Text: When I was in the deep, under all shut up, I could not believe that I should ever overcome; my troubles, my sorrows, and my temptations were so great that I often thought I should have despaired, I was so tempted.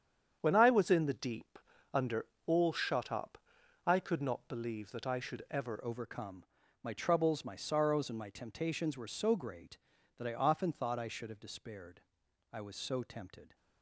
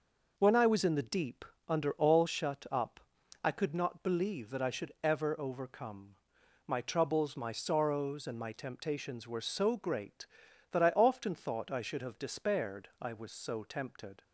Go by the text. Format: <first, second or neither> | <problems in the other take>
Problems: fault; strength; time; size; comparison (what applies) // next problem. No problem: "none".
second | starts louder than the rest; strong; until 1.4 s; 8.5 dB // pauses between "under" and "all"; slight; at 2.2 s; 0.18 s long // changes voice at "overcome"; from 5.8 s on; 7.7 s long